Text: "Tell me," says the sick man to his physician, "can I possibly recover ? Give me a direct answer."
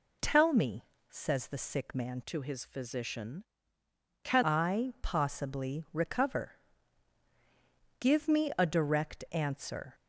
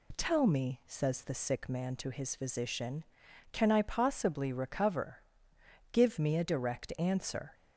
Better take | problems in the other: second | changes voice from "to" to "can"; from 2.2 to 4.4 s; 2.2 s long

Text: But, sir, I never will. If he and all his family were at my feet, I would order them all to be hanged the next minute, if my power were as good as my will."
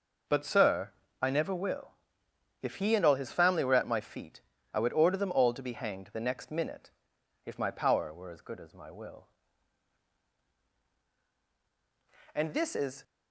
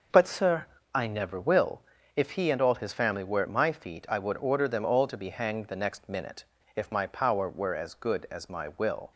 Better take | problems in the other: second | goes on to say "And this is"; noticeable; from 12.3 s on; 0.70 s long

